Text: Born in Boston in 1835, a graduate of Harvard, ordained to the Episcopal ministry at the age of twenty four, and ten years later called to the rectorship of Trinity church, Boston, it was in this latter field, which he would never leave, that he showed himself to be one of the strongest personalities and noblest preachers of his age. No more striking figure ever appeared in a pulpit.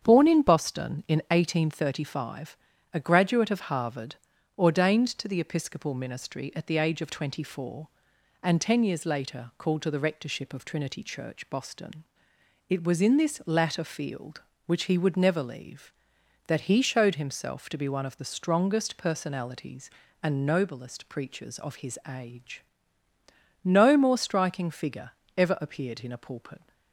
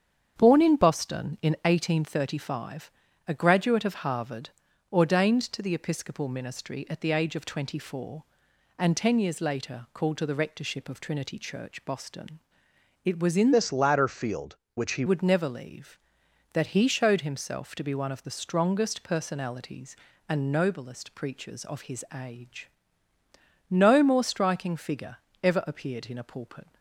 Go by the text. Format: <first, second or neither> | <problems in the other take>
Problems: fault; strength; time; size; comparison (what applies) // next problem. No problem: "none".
first | starts louder than the rest; strong; until 1.3 s; 8 dB; strong in the first // changes voice from "this" to "he"; from 13.5 to 15.0 s; 1.5 s long // pauses between "figure" and "ever"; slight; at 25.1 s; 0.26 s long; slight in the first